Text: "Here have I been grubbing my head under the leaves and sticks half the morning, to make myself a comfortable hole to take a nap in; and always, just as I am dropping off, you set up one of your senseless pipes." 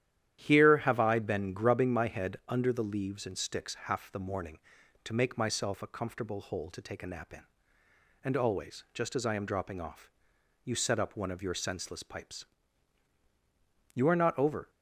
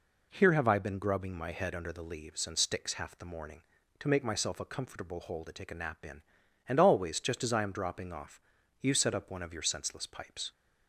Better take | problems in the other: second | starts louder than the rest; strong; until 1.5 s; 11 dB // goes on to say "You are not over"; noticeable; from 13.9 s on; 0.76 s long

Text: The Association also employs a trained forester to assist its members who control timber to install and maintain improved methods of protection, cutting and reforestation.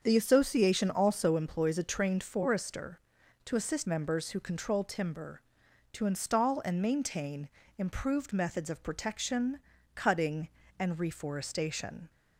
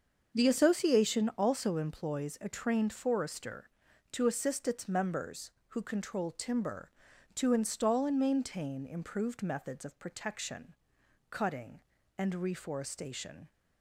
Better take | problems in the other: second | starts louder than the rest; until 1.0 s; 6.5 dB; also in the second // skips "its"; at 3.8 s // pauses between "maintain" and "improved"; slight; at 7.4 s; 0.30 s long

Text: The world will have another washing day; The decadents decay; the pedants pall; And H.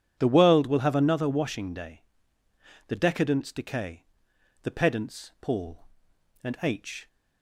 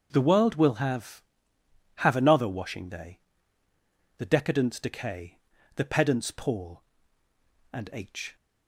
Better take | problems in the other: first | starts louder than the rest; until 1.1 s; 6.5 dB // says "have" twice; at 1.9 s

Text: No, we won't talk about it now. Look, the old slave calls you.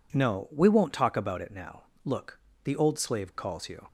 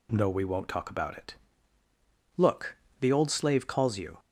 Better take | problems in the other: first | skips "now"; at 1.8 s

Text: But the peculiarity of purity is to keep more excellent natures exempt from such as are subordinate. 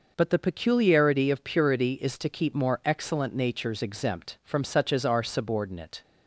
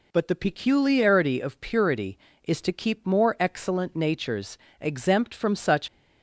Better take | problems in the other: first | pauses between "natures" and "exempt"; slight; at 4.5 s; 0.24 s long // stops before "as are subordinate"; at 5.8 s

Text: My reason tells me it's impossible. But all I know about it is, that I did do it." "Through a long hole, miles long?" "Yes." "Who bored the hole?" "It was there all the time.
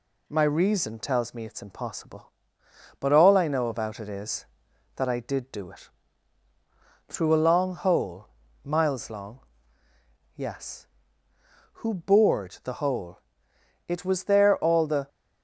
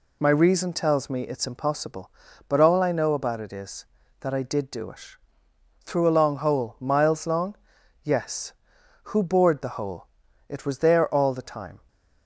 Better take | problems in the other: second | stops before "time"; at 15.0 s

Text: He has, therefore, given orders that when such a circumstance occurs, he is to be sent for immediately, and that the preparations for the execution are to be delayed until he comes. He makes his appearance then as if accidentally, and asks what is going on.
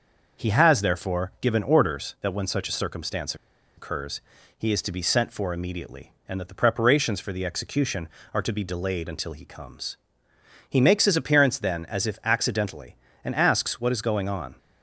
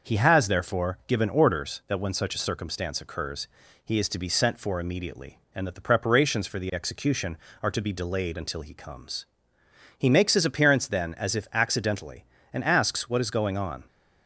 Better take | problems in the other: second | pauses between "circumstance" and "occurs"; at 3.3 s; 0.42 s long

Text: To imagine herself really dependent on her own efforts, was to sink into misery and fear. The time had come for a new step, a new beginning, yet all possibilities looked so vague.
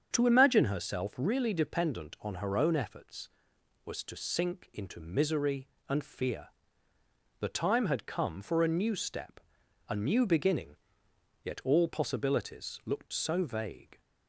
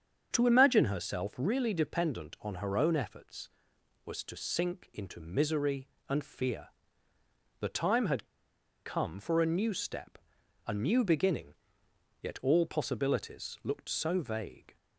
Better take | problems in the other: first | starts louder than the rest; strong; until 1.3 s; 7 dB; strong in the first // pauses between "had" and "come"; noticeable; at 8.2 s; 0.59 s long

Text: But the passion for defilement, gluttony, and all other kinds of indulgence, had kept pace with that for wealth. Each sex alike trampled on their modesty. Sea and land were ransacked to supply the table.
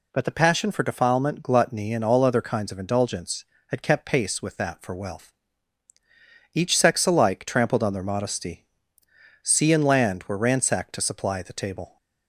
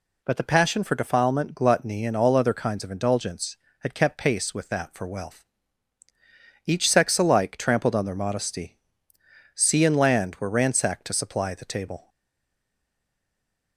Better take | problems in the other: first | stays silent after the last word; noticeable; from 12.0 s on; 1.7 s long

